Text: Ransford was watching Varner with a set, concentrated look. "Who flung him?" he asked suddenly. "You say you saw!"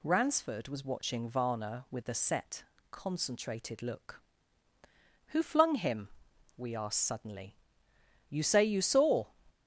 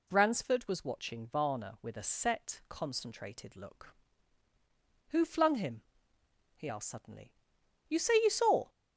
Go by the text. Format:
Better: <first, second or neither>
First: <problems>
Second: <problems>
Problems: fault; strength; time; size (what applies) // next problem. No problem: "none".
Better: second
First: says "we" for "he"; at 6.5 s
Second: none